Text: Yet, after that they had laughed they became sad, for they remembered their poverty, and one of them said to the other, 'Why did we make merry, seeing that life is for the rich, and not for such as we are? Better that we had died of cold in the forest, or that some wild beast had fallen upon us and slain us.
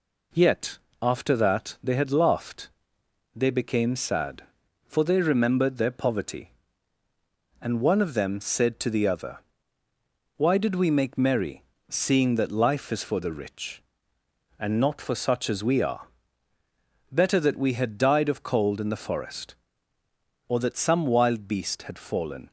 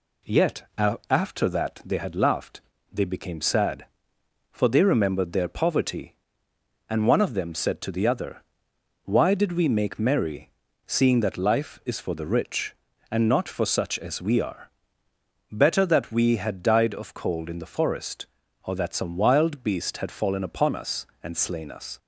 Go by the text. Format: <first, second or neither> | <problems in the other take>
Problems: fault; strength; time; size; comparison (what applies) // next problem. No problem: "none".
second | pauses between "laughed" and "they"; noticeable; at 2.6 s; 0.64 s long; slight in the second // stops before "upon us and slain us"; at 22.4 s